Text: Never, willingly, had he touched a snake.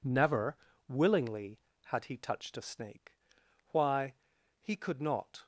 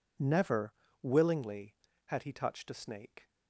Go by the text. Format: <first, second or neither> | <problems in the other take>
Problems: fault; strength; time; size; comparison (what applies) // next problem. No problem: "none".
second | goes on to say "Why he could not"; strong; from 3.7 s on; 1.7 s long